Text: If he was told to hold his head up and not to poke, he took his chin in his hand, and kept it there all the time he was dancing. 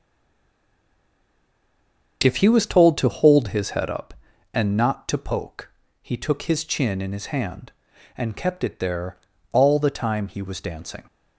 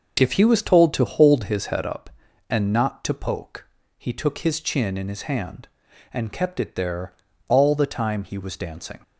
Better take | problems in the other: second | stays silent before the first word; until 2.2 s; 2.2 s long // starts louder than the rest; until 3.2 s; 6.5 dB; also in the second // pauses between "there" and "all"; slight; at 9.1 s; 0.34 s long; slight in the second

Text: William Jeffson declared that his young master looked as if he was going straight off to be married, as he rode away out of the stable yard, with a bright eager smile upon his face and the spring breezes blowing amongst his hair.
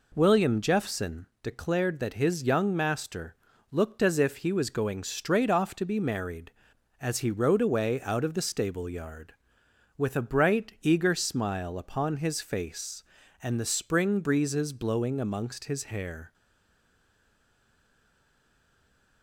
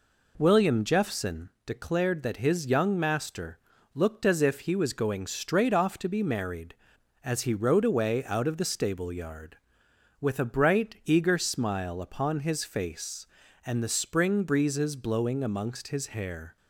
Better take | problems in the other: second | pauses between "Jeffson" and "declared"; slight; at 1.2 s; 0.16 s long; slight in the second // pauses between "master" and "looked"; slight; at 3.3 s; 0.36 s long; slight in the second // stays silent after the last word; strong; from 16.3 s on; 2.9 s long

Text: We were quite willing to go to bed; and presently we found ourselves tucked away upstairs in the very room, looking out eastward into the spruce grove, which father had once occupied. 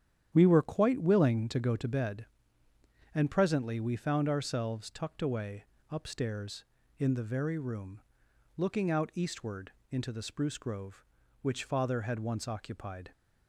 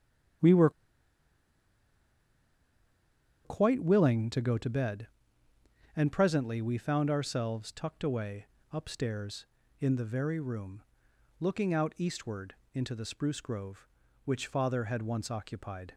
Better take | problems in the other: first | starts louder than the rest; strong; until 4.1 s; 9.5 dB; strong in the first // pauses between "were" and "quite"; strong; at 0.6 s; 2.7 s long // pauses between "away" and "upstairs"; slight; at 8.4 s; 0.26 s long; slight in the first // pauses between "eastward" and "into"; slight; at 12.5 s; 0.18 s long; slight in the first

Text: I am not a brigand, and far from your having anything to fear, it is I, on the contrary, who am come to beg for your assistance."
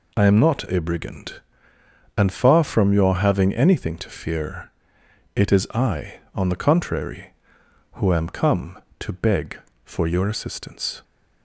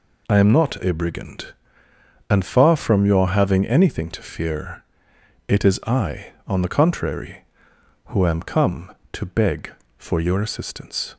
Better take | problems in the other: neither | none

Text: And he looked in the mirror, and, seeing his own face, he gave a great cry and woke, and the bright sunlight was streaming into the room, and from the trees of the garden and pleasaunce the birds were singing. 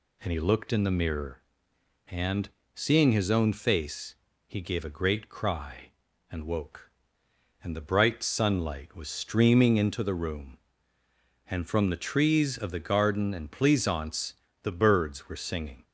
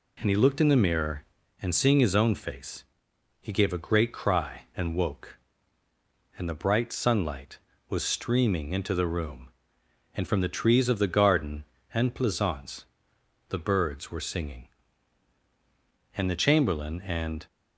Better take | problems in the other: first | pauses between "pleasaunce" and "the"; noticeable; at 12.8 s; 0.66 s long; slight in the first // goes on to say "And the Chamberlain and"; noticeable; from 16.1 s on; 1.3 s long

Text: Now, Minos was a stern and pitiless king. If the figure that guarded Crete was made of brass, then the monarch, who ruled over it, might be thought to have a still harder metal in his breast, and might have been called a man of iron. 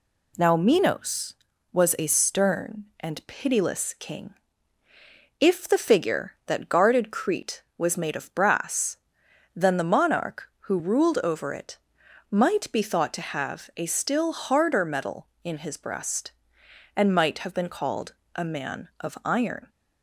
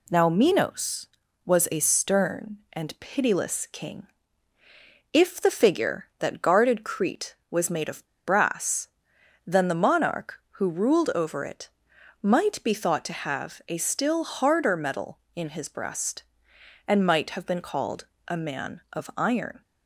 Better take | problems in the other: first | pauses between "of" and "brass"; slight; at 8.0 s; 0.20 s long // pauses between "called" and "a"; slight; at 18.0 s; 0.20 s long; slight in the first

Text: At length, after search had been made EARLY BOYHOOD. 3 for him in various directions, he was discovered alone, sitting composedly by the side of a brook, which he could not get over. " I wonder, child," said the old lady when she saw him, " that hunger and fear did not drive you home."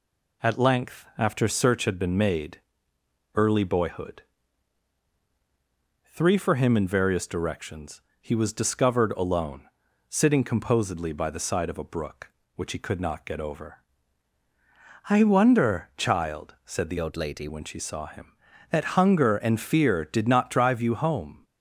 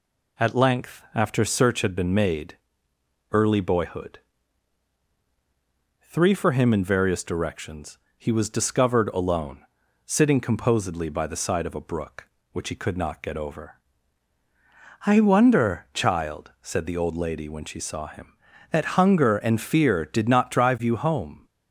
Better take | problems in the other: second | pauses between "made" and "EARLY"; noticeable; at 2.5 s; 0.76 s long; noticeable in the second // changes voice from "old" to "lady"; from 16.9 to 17.4 s; 0.5 s long

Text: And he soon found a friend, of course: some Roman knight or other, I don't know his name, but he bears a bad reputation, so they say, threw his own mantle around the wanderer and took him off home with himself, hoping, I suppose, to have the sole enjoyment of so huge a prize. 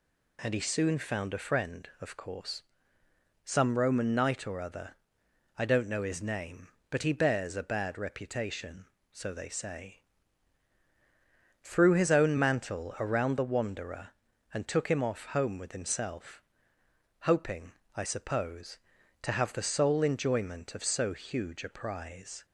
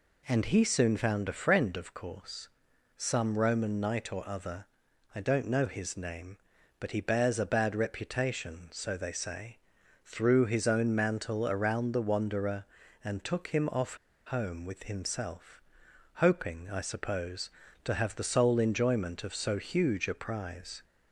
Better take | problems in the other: first | pauses between "off" and "home"; slight; at 13.9 s; 0.30 s long

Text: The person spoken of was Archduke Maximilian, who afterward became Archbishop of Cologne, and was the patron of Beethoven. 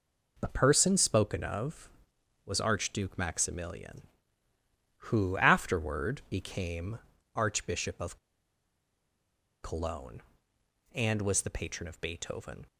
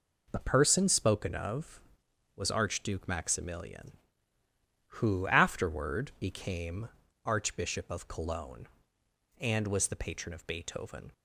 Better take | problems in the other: second | pauses between "became" and "Archbishop"; slight; at 6.9 s; 0.34 s long; slight in the second // pauses between "of" and "Cologne"; strong; at 8.1 s; 1.4 s long

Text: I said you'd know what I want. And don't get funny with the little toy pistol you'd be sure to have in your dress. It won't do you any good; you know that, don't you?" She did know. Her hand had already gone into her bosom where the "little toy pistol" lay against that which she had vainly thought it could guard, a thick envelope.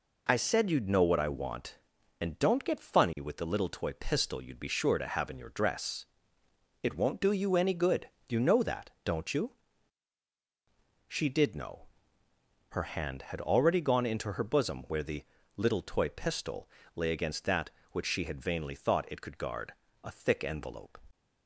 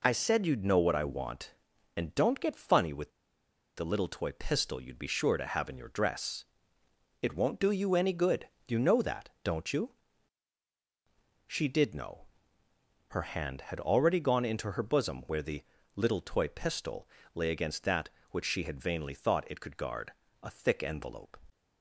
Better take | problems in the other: first | pauses between "with" and "the"; noticeable; at 3.0 s; 0.69 s long // pauses between "the" and "little"; slight; at 15.6 s; 0.32 s long; slight in the first // pauses between "pistol" and "lay"; slight; at 17.0 s; 0.26 s long; slight in the first

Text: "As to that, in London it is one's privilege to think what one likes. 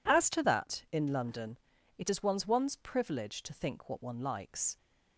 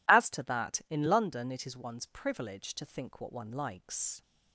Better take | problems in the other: second | pauses between "London" and "it"; at 1.5 s; 0.40 s long // says "one's" twice; at 2.4 s

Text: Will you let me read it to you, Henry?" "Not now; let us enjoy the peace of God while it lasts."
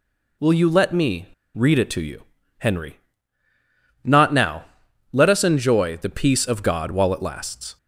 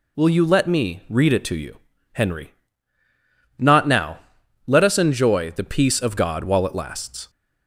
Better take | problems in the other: second | pauses between "me" and "read"; slight; at 1.2 s; 0.28 s long

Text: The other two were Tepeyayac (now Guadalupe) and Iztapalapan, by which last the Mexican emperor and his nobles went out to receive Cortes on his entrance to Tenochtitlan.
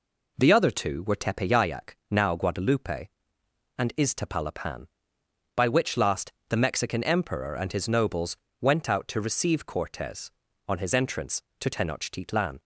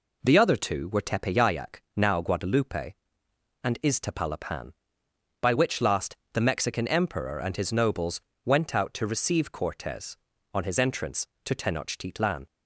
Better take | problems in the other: neither | pauses between "last" and "the"; slight; the same in both // pauses between "nobles" and "went"; slight; the same in both

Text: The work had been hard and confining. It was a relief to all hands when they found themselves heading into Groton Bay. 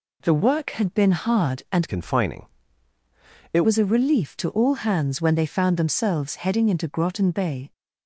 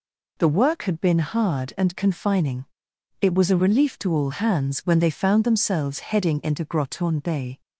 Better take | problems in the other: second | changes voice from "confining" to "It"; from 1.8 to 3.6 s; 1.8 s long

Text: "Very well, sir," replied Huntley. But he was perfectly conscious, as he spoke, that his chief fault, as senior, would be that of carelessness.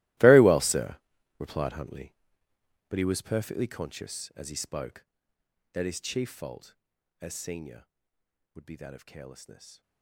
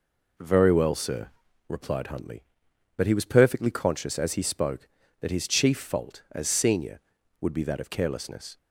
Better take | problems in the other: second | gets quieter; strong; throughout; 19 dB

